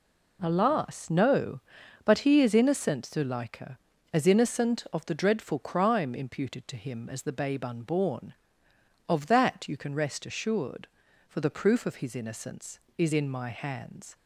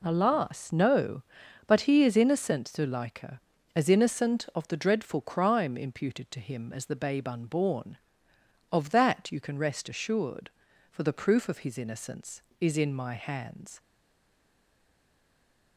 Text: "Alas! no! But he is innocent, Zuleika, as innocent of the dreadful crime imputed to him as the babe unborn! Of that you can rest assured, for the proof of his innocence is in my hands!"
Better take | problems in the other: first | stays silent after the last word; noticeable; from 13.7 s on; 2.0 s long

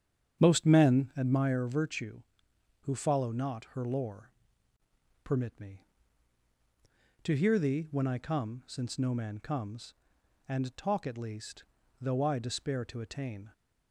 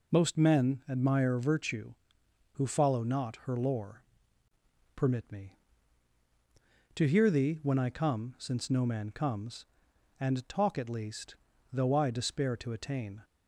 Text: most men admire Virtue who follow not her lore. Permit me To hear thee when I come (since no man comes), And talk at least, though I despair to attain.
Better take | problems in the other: second | starts louder than the rest; strong; until 1.5 s; 8.5 dB

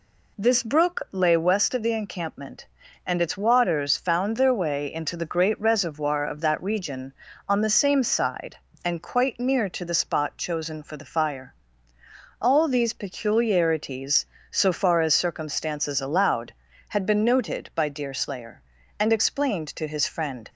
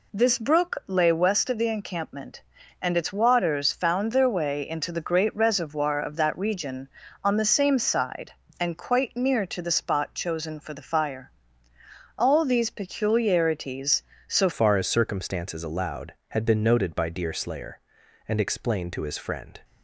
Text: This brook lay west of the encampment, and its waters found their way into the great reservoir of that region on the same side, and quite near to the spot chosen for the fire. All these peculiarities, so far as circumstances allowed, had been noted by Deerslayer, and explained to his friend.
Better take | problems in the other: first | changes voice at "far"; from 14.5 s on; 5.0 s long

